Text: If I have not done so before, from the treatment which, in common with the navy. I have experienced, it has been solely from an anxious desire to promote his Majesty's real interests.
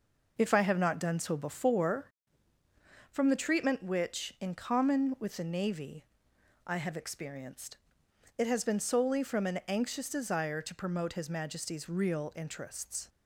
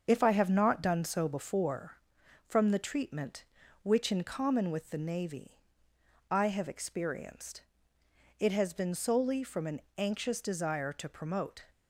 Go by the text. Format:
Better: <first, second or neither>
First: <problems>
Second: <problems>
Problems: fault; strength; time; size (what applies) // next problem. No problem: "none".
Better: first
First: none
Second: starts louder than the rest; until 1.0 s; 6.5 dB // pauses between "an" and "anxious"; slight; at 9.7 s; 0.18 s long // stops before "his Majesty's real interests"; at 11.7 s